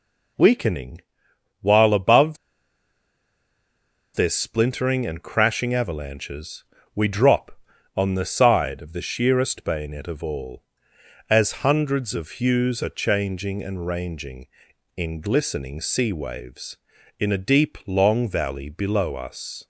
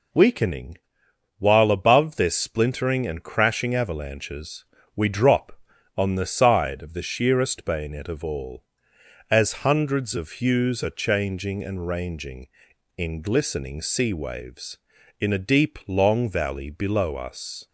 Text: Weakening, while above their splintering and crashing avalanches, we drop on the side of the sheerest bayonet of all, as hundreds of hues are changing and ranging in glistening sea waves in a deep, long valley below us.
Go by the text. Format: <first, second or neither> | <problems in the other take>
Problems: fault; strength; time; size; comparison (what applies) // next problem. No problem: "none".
second | pauses between "above" and "their"; strong; at 2.3 s; 1.7 s long